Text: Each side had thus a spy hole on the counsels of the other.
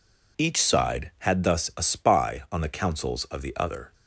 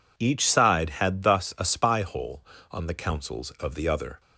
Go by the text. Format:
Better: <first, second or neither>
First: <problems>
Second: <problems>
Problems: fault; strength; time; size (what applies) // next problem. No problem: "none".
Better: second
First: skips "hole"; at 2.4 s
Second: none